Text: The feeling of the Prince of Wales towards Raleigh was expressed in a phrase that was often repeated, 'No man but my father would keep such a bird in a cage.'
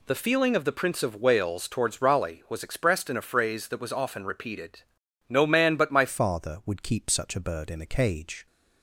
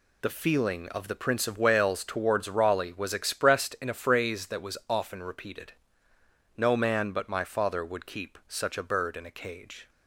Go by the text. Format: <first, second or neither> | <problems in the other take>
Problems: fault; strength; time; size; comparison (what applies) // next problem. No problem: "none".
second | changes voice at "father"; from 6.0 s on; 2.4 s long